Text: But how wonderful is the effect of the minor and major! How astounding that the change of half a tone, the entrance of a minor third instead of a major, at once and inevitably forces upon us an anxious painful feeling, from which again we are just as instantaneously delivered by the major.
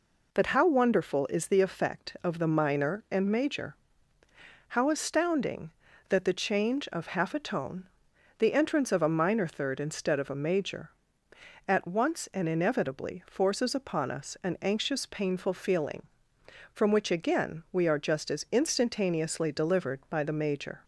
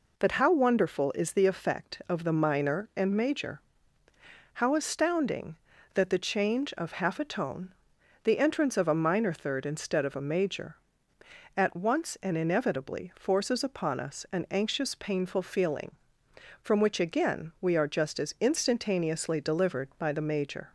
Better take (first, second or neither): neither